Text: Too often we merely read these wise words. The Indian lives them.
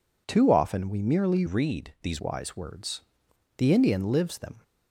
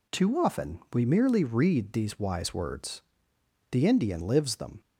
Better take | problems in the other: second | changes voice from "read" to "these"; from 1.4 to 2.2 s; 0.8 s long

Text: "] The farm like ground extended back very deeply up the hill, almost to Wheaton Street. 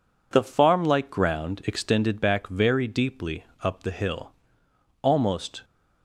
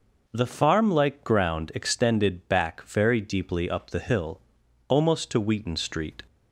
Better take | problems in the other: second | pauses between "deeply" and "up"; slight; at 3.4 s; 0.16 s long // stops before "to Wheaton Street"; at 5.6 s

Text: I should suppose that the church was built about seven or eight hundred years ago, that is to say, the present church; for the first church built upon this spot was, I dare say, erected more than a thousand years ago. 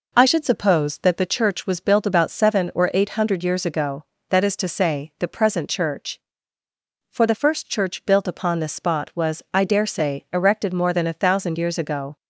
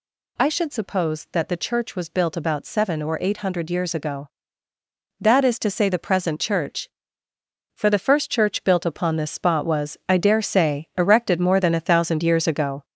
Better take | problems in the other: first | gets louder; noticeable; throughout; 4 dB

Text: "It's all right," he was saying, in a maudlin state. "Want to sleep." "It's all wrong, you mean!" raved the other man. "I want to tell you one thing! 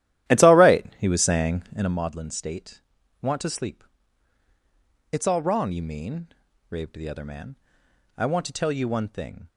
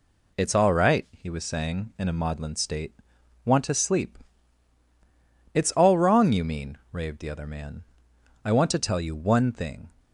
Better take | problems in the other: second | starts louder than the rest; strong; until 2.0 s; 12.5 dB

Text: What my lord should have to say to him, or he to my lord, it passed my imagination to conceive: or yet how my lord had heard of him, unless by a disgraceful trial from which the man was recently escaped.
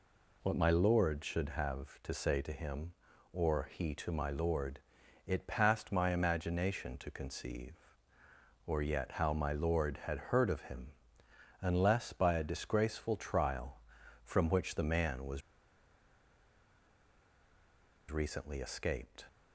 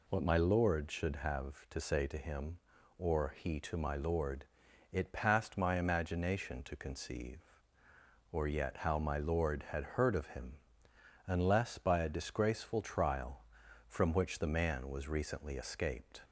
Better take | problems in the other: second | pauses between "was" and "recently"; strong; at 15.4 s; 2.7 s long

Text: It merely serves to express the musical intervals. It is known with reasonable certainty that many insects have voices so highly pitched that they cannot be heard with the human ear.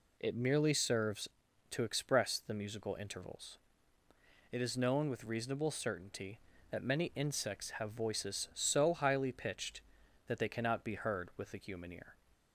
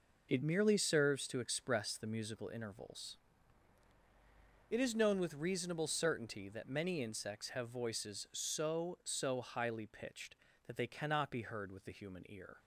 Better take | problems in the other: first | says "so" twice; at 9.0 s

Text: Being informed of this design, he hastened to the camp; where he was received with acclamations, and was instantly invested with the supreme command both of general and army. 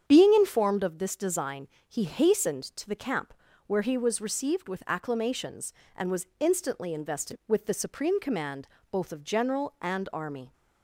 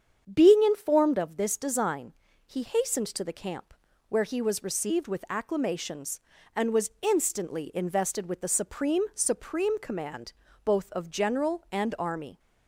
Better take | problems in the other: first | starts louder than the rest; strong; until 1.3 s; 8 dB; strong in the first // says "supreme" twice; at 9.1 s // pauses between "command" and "both"; slight; at 10.3 s; 0.30 s long; slight in the first

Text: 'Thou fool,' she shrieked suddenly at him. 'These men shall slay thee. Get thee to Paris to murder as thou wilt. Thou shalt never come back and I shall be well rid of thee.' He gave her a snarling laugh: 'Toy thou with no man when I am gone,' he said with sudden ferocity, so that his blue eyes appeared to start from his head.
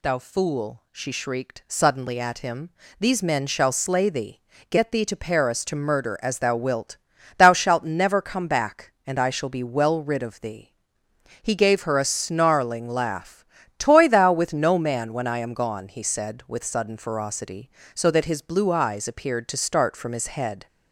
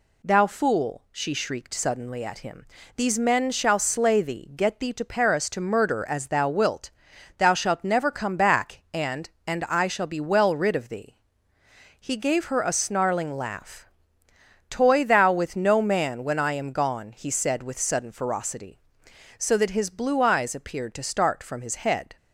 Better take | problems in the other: first | says "and" twice; at 9.4 s

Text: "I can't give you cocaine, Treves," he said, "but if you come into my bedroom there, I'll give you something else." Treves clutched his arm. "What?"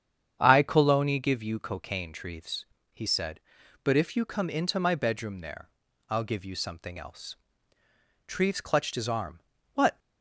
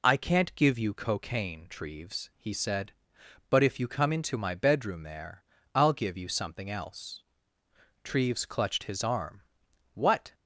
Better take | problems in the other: second | starts louder than the rest; strong; until 1.4 s; 8.5 dB // says "coloni" for "can't"; at 0.6 s

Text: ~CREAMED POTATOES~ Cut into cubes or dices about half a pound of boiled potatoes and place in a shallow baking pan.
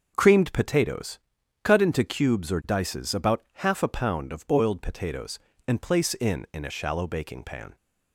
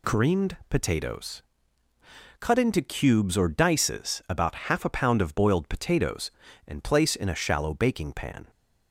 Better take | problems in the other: second | starts louder than the rest; until 1.1 s; 6.5 dB // says "in" twice; at 6.5 s

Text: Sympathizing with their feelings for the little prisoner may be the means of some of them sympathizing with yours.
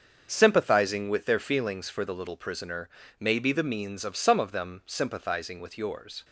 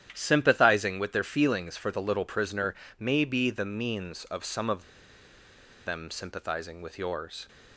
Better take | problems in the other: first | starts louder than the rest; strong; until 1.1 s; 10.5 dB; also in the first // pauses between "prisoner" and "may"; slight; at 2.7 s; 0.24 s long; slight in the first // pauses between "of" and "them"; at 4.8 s; 1.0 s long

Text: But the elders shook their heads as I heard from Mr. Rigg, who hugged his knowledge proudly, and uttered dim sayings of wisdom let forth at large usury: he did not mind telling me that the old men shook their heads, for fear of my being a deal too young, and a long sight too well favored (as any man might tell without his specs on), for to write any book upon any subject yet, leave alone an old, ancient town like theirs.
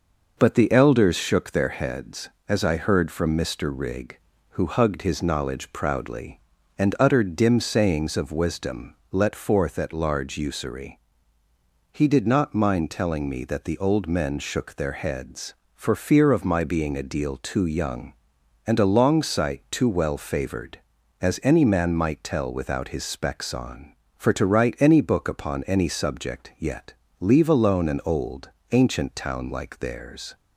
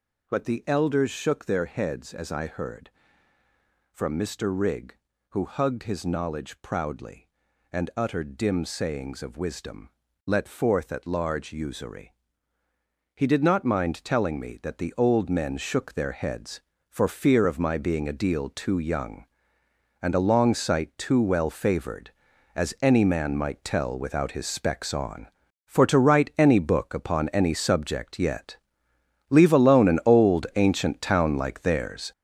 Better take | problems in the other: first | gets louder; strong; throughout; 8 dB // pauses between "wisdom" and "let"; slight; at 9.8 s; 0.36 s long; slight in the first

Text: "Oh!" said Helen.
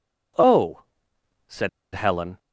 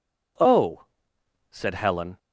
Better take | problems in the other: second | pauses between "said" and "Helen"; slight; at 1.6 s; 0.24 s long

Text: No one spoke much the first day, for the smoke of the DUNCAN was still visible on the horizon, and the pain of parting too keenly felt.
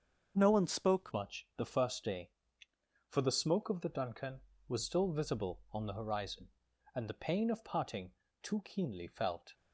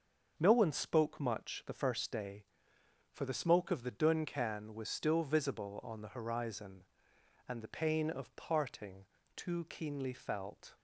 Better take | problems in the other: second | starts louder than the rest; until 1.3 s; 6.5 dB; also in the second // changes voice at "much"; from 1.1 s on; 8.4 s long // pauses between "parting" and "too"; slight; at 8.1 s; 0.28 s long; slight in the second

